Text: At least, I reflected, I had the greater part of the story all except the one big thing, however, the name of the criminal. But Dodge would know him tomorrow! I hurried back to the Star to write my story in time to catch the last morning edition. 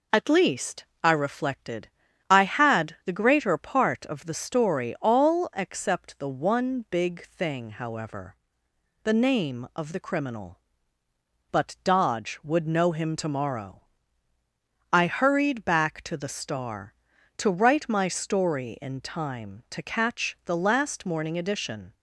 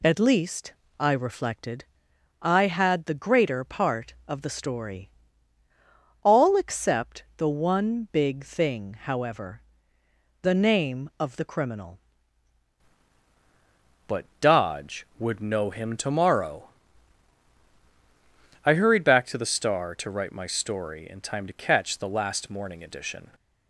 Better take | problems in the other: first | pauses between "story" and "all"; at 5.0 s; 1.1 s long // changes voice at "But"; from 14.0 s on; 9.2 s long // pauses between "But" and "Dodge"; slight; at 14.2 s; 0.16 s long

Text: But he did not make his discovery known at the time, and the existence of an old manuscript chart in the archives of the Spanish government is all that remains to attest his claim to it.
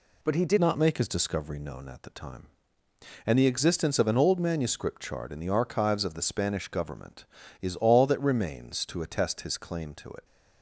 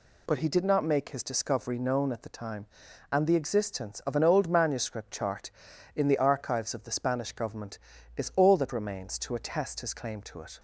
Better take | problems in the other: second | changes voice at "not"; from 0.5 s on; 9.7 s long

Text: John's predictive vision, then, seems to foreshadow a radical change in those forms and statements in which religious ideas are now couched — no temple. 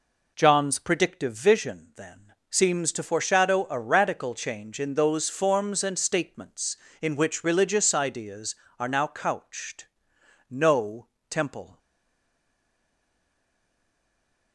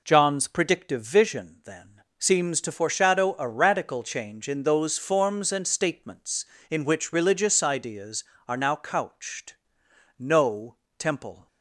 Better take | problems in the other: second | pauses between "no" and "temple"; slight; at 11.0 s; 0.24 s long; slight in the second // stays silent after the last word; strong; from 11.7 s on; 2.8 s long

